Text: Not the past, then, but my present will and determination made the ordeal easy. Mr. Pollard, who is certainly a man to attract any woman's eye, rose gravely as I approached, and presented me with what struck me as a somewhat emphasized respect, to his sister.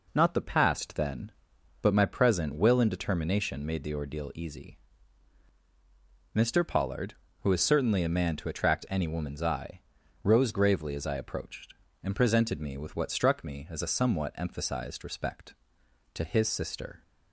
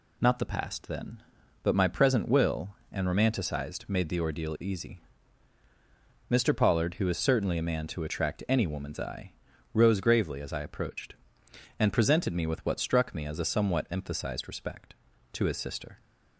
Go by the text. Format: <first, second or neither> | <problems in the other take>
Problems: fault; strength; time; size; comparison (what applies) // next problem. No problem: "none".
first | says "romanticized" for "determination"; at 3.0 s